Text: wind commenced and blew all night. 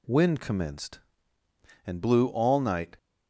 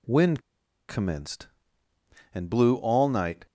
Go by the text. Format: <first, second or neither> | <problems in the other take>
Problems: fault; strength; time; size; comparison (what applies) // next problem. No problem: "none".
first | pauses between "wind" and "commenced"; noticeable; at 0.3 s; 0.49 s long